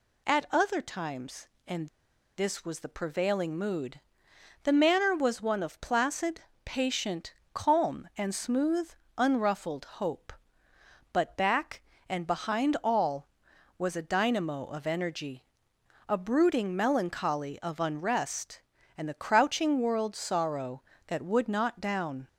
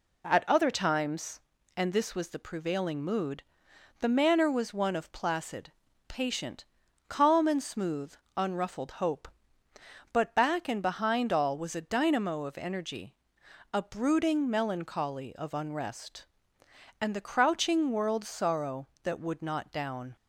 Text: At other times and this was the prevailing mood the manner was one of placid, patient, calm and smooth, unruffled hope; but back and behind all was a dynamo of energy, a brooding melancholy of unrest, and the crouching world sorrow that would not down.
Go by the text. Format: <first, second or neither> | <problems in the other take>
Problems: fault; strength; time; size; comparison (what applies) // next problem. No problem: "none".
second | pauses between "and" and "this"; noticeable; at 1.8 s; 0.48 s long // pauses between "mood" and "the"; noticeable; at 3.9 s; 0.62 s long; noticeable in the second